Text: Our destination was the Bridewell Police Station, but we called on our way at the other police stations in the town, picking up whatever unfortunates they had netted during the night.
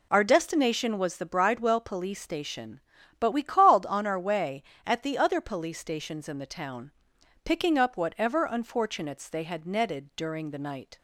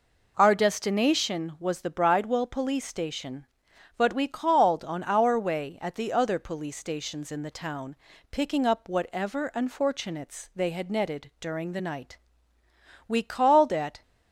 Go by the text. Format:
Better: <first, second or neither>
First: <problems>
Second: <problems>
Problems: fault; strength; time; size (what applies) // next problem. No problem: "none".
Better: first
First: none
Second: goes on to say "We called at"; noticeable; from 13.0 s on; 0.94 s long